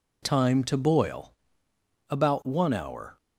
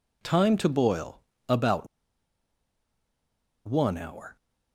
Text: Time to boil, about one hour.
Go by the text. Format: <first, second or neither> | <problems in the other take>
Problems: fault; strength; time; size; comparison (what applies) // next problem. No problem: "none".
first | pauses between "about" and "one"; strong; at 1.8 s; 1.8 s long